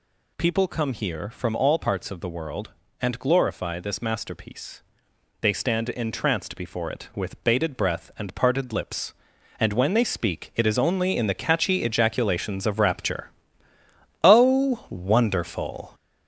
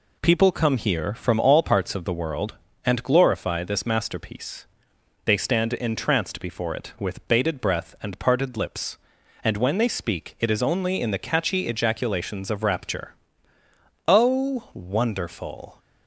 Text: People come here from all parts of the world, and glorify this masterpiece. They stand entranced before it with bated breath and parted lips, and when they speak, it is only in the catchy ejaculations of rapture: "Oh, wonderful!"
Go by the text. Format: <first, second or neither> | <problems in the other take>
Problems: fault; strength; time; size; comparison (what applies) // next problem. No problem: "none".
second | gets louder; noticeable; throughout; 5 dB